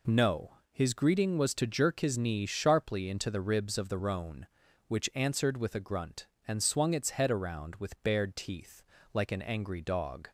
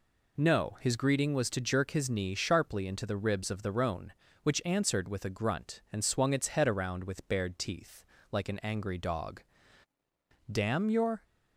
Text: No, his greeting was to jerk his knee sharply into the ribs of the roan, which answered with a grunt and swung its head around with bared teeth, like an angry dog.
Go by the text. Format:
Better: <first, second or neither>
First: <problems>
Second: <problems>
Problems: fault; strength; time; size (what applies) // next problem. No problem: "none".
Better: first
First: none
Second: goes on to say "Damn your"; noticeable; from 10.5 s on; 0.72 s long